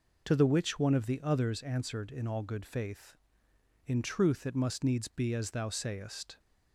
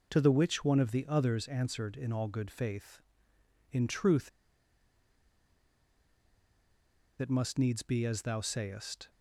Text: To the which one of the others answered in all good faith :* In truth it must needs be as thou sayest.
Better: first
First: none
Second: pauses between "truth" and "it"; strong; at 4.2 s; 2.9 s long

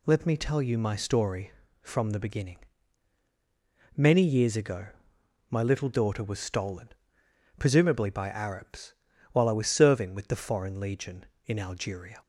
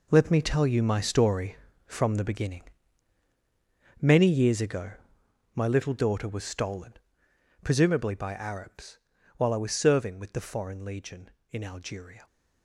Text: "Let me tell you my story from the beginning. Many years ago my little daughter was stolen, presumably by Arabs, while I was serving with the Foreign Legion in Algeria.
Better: first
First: pauses between "ago" and "my"; noticeable; at 4.8 s; 0.62 s long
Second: gets quieter; strong; throughout; 11.5 dB // pauses between "ago" and "my"; noticeable; at 4.9 s; 0.62 s long

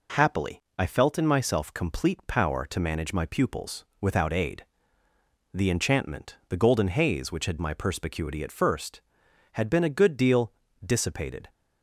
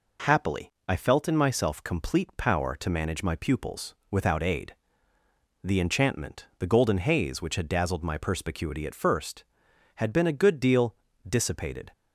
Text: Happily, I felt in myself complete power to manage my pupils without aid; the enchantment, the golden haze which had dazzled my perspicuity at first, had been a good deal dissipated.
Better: second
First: pauses between "pupils" and "without"; slight; at 3.8 s; 0.16 s long // skips "dazzled"; at 7.5 s // pauses between "deal" and "dissipated"; slight; at 10.5 s; 0.32 s long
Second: pauses between "pupils" and "without"; slight; at 3.9 s; 0.16 s long // pauses between "deal" and "dissipated"; slight; at 10.9 s; 0.32 s long

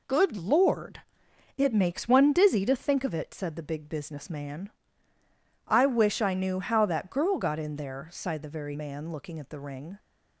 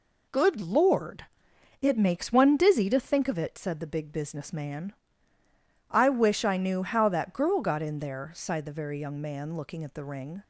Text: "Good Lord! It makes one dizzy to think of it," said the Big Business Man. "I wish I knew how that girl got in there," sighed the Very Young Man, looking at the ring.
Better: second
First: skips "Young"; at 8.7 s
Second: none

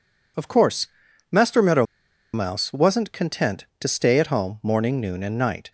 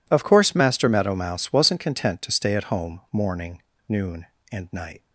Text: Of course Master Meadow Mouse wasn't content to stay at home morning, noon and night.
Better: second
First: pauses between "course" and "Master"; at 0.8 s; 0.44 s long // pauses between "Meadow" and "Mouse"; noticeable; at 1.8 s; 0.49 s long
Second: none

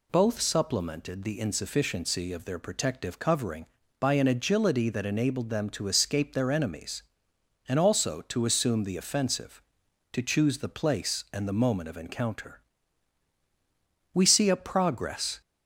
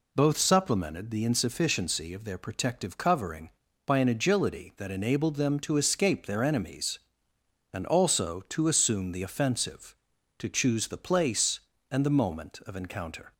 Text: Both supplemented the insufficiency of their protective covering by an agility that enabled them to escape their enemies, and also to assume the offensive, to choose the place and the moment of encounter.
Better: second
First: goes on to say "We see a progress"; noticeable; from 14.1 s on; 1.2 s long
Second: none

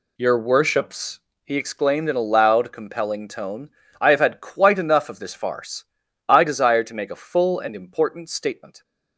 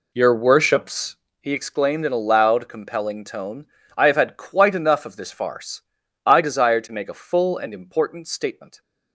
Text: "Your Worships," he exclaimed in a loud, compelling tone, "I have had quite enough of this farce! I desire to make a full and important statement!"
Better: first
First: none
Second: starts louder than the rest; slight; until 1.4 s; 2.5 dB

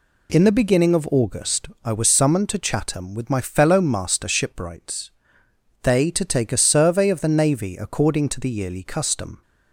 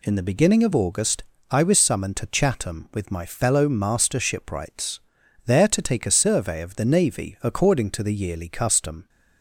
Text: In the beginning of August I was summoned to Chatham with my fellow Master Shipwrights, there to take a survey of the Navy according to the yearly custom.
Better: second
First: pauses between "August" and "I"; slight; at 1.6 s; 0.16 s long // says "they" for "there"; at 5.8 s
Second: pauses between "August" and "I"; slight; at 1.2 s; 0.26 s long

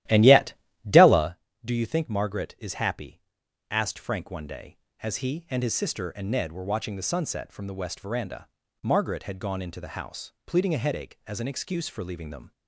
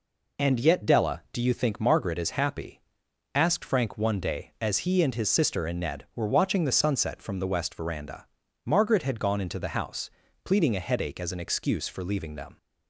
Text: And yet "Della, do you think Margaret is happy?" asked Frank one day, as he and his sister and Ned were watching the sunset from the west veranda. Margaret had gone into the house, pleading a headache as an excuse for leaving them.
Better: second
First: starts louder than the rest; strong; until 1.3 s; 13.5 dB // pauses between "yet" and "Della"; slight; at 0.5 s; 0.34 s long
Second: none

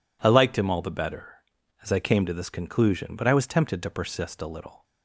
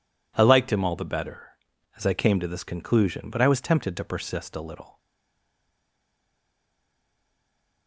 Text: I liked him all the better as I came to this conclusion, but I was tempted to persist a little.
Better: first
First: none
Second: stays silent after the last word; strong; from 4.9 s on; 2.9 s long

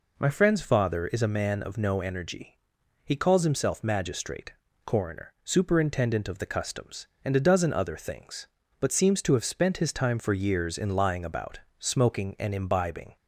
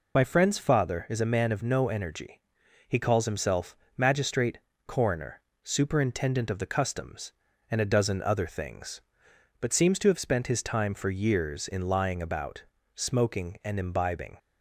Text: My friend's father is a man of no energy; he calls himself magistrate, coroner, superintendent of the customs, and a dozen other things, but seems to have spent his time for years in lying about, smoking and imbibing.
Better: first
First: none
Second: loses the start of "My"; at 0.1 s; 30 ms // pauses between "himself" and "magistrate"; slight; at 3.7 s; 0.22 s long

